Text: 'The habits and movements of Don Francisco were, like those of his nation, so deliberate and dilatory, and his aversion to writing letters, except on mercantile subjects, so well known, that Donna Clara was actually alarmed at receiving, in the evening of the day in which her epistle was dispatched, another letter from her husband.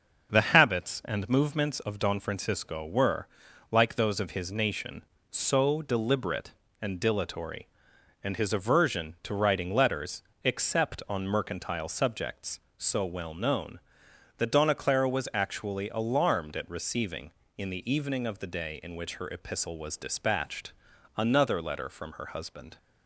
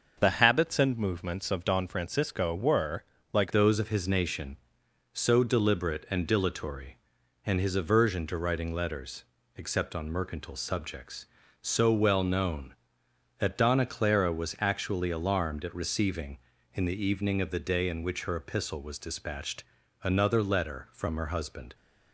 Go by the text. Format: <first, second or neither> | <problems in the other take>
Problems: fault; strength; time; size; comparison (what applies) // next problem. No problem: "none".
first | starts louder than the rest; noticeable; until 1.2 s; 6 dB; also in the first // changes voice at "those"; from 3.5 s on; 18.2 s long